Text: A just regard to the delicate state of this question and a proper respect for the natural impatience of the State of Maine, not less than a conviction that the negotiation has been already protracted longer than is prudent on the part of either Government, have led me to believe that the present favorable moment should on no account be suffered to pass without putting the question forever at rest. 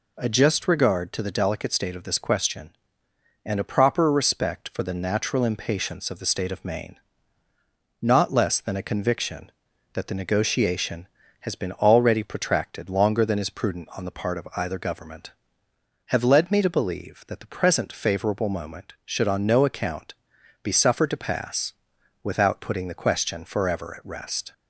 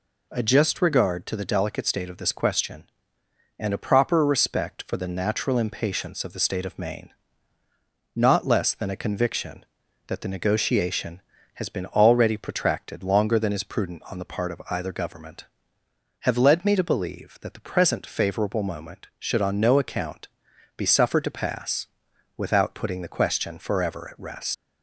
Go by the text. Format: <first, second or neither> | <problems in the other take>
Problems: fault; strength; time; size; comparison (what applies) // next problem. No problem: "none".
first | pauses between "account" and "be"; noticeable; at 20.2 s; 0.50 s long; noticeable in the first // pauses between "pass" and "without"; noticeable; at 21.8 s; 0.50 s long; noticeable in the first // leaves "rest" unfinished; at 24.5 s; 115 ms